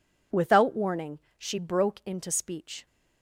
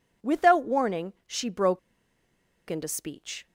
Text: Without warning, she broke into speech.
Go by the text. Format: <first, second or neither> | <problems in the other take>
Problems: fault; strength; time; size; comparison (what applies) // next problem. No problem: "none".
first | pauses between "broke" and "into"; noticeable; at 1.7 s; 0.90 s long